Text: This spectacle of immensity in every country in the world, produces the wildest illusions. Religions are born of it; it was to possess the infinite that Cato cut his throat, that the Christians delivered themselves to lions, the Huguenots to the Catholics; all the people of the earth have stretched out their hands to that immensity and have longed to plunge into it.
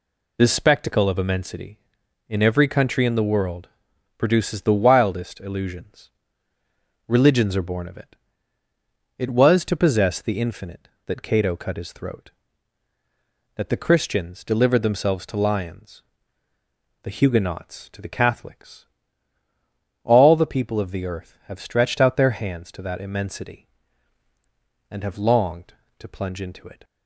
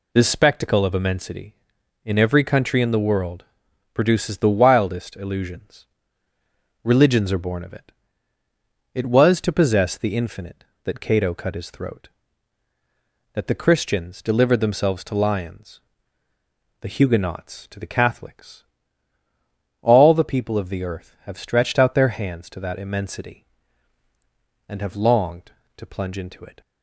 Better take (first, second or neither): neither